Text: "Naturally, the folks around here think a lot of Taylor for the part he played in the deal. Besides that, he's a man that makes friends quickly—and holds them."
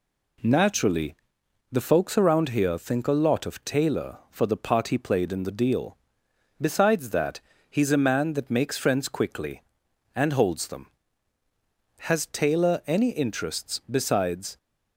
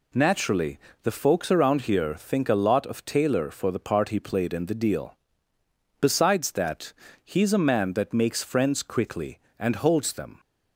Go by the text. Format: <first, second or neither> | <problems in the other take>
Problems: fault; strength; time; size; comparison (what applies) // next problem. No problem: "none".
second | goes on to say "Has Taylor any interests besides"; strong; from 12.0 s on; 2.5 s long